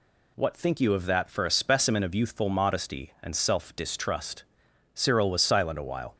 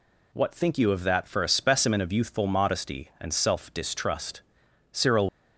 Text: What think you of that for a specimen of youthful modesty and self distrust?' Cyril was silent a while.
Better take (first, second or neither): first